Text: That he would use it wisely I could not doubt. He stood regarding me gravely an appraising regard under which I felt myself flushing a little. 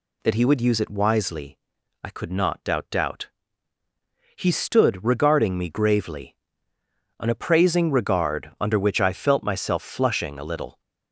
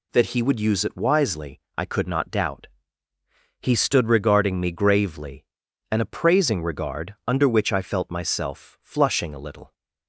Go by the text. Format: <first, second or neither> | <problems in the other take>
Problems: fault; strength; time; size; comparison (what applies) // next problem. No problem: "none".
second | pauses between "wisely" and "I"; noticeable; at 1.5 s; 0.48 s long; slight in the second // says "doubt" twice; at 2.9 s // pauses between "gravely" and "an"; noticeable; at 6.3 s; 0.82 s long; noticeable in the second